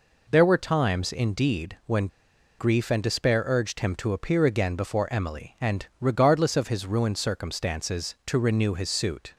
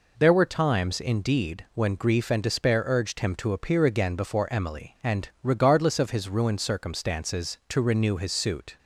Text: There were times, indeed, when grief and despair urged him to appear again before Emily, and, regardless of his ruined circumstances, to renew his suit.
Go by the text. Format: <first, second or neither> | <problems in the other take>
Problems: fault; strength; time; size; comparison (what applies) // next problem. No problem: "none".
second | pauses between "when" and "grief"; noticeable; at 2.0 s; 0.51 s long